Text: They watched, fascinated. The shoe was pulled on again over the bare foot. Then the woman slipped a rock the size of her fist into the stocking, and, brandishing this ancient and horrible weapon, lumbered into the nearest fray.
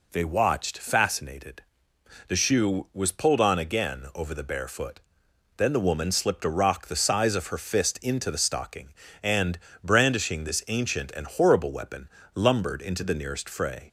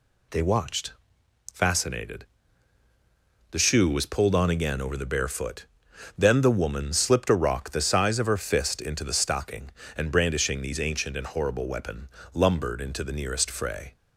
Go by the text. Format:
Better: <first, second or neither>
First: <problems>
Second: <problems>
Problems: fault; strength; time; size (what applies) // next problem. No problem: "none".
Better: first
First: none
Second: says "these" for "this"; at 10.6 s